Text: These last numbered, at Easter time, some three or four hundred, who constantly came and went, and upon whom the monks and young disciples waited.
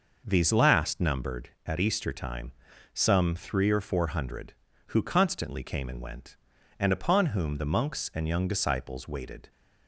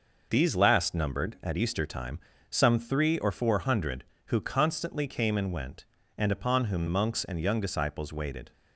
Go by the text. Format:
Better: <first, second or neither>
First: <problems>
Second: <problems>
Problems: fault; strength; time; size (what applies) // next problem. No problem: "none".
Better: first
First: none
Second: skips "the"; at 6.8 s